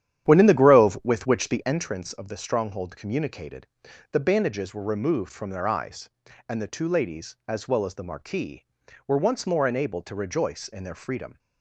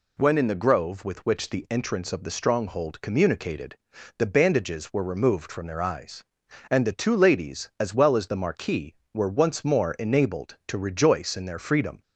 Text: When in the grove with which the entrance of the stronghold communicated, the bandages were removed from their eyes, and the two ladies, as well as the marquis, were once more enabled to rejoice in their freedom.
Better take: second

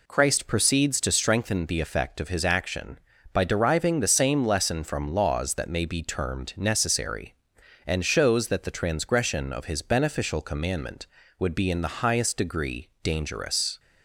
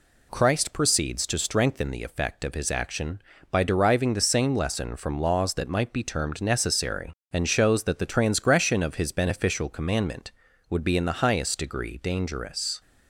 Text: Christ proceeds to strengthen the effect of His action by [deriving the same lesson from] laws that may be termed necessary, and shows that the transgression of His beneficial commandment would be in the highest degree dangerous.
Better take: first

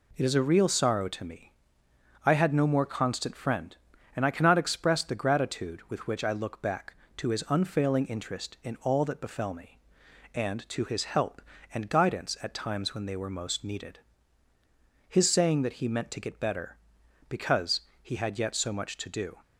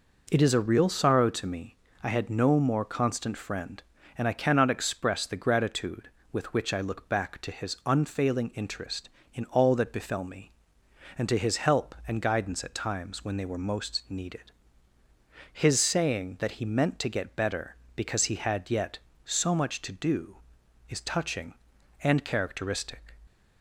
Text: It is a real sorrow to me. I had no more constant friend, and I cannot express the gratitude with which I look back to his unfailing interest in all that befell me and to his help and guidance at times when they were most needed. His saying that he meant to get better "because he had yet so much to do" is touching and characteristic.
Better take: second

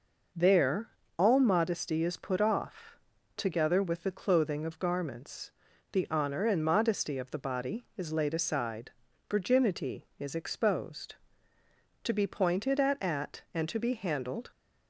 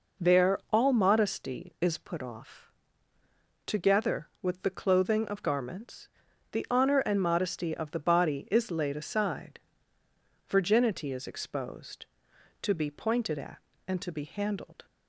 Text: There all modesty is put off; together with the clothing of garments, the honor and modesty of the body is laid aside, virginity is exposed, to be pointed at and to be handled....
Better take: second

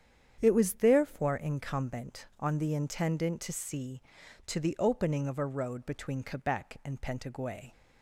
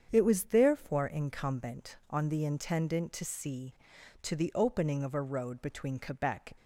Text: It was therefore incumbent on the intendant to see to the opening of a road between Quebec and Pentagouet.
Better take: first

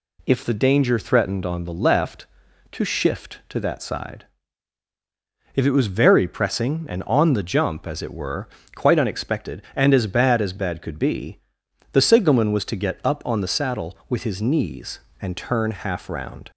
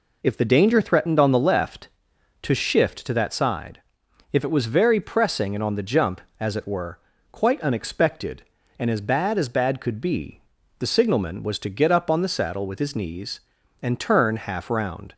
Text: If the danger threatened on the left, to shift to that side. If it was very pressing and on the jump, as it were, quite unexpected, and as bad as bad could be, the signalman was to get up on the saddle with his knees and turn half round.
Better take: neither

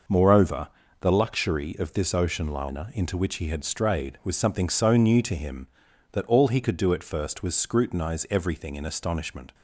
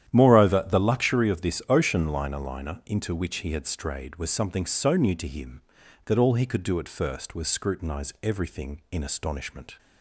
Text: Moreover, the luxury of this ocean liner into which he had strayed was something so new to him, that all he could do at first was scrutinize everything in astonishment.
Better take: first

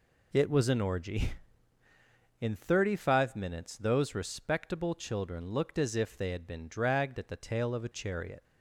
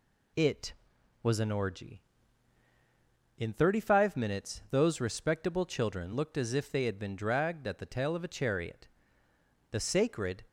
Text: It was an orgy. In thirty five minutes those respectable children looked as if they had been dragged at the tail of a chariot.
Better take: first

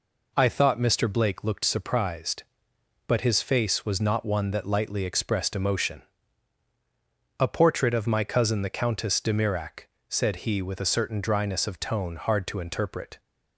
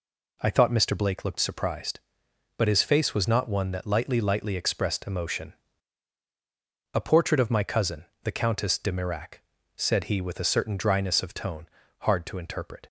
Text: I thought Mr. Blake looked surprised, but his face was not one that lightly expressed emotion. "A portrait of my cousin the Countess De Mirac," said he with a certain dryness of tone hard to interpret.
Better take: first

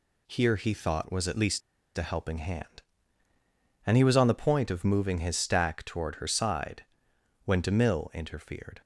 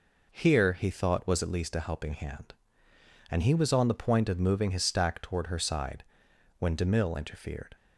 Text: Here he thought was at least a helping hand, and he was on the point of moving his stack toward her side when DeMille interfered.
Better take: second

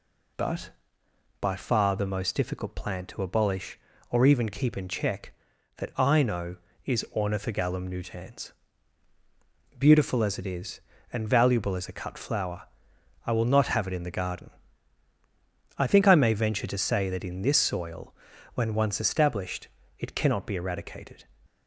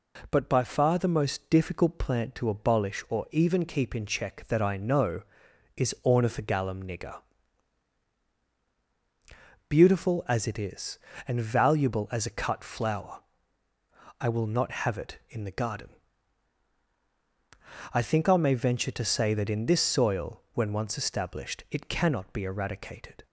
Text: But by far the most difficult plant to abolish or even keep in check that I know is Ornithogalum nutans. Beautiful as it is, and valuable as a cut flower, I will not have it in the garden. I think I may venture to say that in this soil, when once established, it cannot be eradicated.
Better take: first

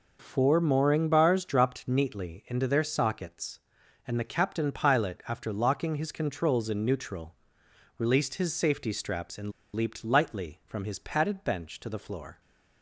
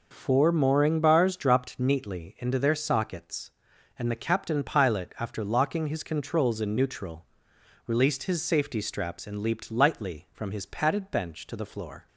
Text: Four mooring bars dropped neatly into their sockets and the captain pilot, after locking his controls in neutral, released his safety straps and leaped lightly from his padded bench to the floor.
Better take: second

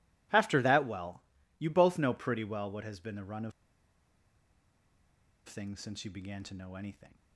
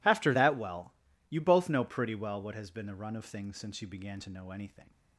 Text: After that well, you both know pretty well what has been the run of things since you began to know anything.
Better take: second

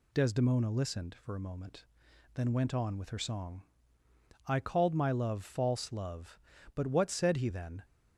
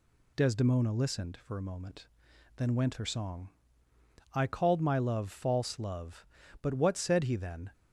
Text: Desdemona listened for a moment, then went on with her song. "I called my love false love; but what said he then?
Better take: first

